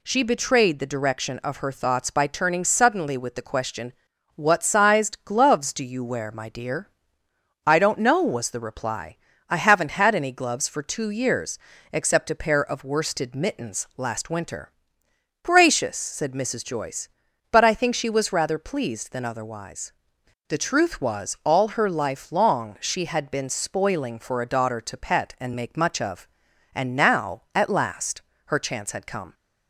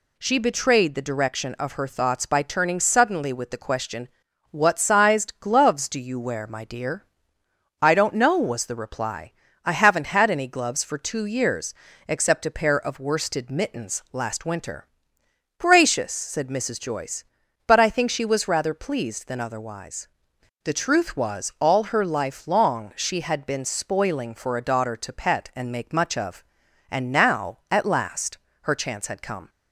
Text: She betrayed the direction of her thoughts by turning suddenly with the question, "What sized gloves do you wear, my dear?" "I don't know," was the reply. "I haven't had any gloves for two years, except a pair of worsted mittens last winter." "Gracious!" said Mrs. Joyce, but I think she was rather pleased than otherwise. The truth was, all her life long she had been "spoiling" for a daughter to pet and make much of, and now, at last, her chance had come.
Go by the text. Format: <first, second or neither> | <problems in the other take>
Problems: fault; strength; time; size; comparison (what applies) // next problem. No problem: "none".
neither | none